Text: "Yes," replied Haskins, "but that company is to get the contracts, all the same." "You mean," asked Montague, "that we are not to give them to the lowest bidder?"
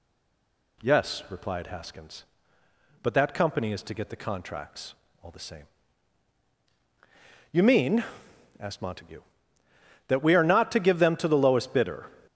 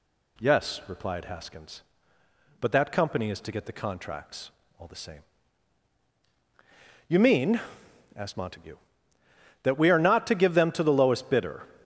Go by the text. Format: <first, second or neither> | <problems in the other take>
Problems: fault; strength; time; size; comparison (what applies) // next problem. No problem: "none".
second | stays silent before the first word; slight; until 0.8 s; 0.8 s long